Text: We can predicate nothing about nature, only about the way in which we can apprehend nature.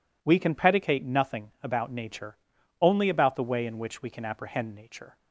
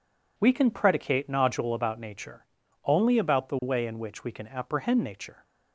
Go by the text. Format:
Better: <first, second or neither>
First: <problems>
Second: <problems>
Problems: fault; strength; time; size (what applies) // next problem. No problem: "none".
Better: first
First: none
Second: says "nodule" for "nothing"; at 1.3 s